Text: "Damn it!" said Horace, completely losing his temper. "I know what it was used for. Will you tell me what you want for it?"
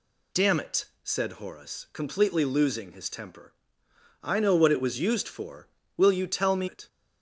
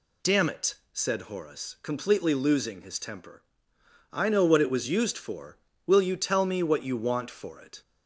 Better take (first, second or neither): second